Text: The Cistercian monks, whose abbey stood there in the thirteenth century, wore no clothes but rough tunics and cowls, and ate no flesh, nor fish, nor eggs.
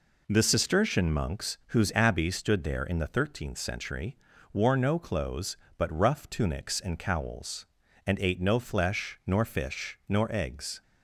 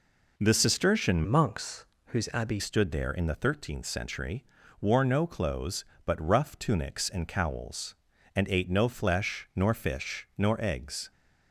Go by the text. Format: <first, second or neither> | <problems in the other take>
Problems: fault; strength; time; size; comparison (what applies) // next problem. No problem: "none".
first | changes voice from "monks" to "abbey"; from 1.2 to 2.5 s; 1.3 s long